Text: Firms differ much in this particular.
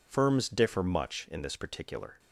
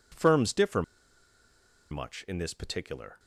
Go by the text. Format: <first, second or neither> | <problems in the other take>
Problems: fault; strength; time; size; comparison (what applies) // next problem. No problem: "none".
first | pauses between "differ" and "much"; at 0.8 s; 1.0 s long